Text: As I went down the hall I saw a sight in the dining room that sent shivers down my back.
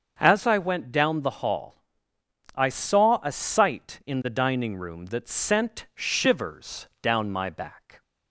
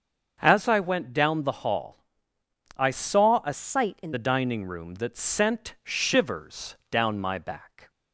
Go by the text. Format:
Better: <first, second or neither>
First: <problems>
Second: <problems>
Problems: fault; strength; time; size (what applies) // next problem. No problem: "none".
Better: first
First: starts louder than the rest; until 1.2 s; 6.5 dB // pauses between "hall" and "I"; noticeable; at 1.7 s; 0.80 s long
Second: starts louder than the rest; until 1.4 s; 6.5 dB // pauses between "hall" and "I"; noticeable; at 1.9 s; 0.80 s long // changes voice from "sight" to "in"; from 3.5 to 4.1 s; 0.6 s long